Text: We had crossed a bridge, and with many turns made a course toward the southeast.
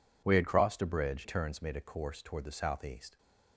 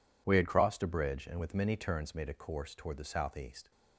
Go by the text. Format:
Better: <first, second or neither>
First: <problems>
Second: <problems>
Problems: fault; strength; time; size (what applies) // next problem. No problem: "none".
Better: second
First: skips "and with many"; at 1.2 s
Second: none